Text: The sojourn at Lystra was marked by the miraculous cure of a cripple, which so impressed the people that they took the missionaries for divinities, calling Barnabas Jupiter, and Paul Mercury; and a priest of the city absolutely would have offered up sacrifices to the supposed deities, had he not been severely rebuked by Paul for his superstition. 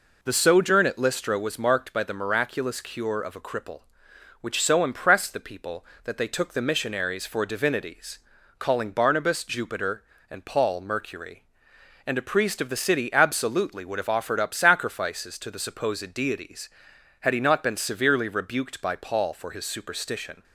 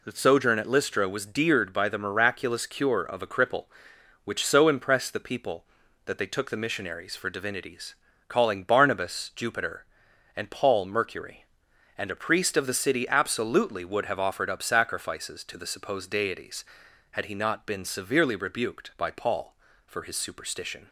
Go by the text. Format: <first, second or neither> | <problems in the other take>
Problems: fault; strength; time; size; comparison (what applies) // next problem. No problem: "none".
first | says "deared" for "marked"; at 1.2 s